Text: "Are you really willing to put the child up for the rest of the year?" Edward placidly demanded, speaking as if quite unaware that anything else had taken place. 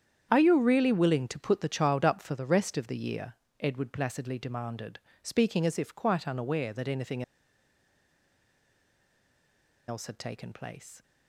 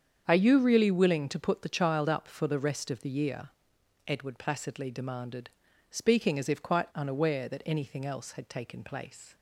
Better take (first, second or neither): second